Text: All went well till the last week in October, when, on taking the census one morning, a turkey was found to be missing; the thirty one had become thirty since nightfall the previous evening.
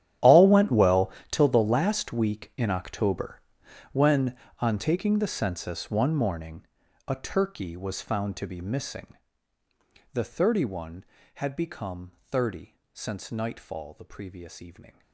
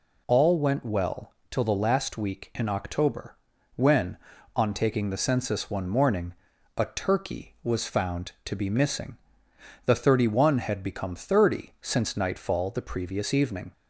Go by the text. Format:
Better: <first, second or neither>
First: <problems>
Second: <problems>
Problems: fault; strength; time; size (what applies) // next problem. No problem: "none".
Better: second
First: gets quieter; strong; throughout; 18.5 dB // pauses between "well" and "till"; slight; at 1.1 s; 0.20 s long // pauses between "thirty" and "since"; slight; at 12.7 s; 0.18 s long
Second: pauses between "well" and "till"; slight; at 1.3 s; 0.16 s long